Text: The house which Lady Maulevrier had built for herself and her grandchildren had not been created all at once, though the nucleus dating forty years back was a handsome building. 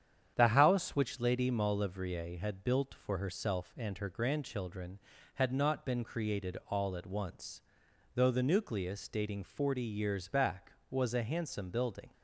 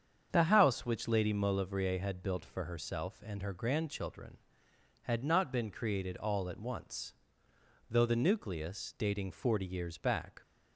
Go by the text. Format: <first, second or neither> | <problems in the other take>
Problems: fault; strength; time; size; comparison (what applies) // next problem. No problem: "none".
first | starts louder than the rest; strong; until 1.3 s; 7.5 dB; strong in the first // stops before "was a handsome building"; at 10.4 s